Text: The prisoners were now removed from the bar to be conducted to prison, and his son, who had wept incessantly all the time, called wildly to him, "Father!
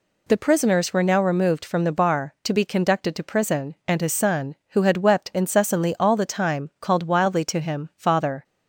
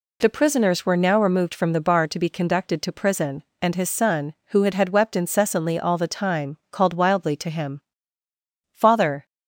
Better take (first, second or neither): first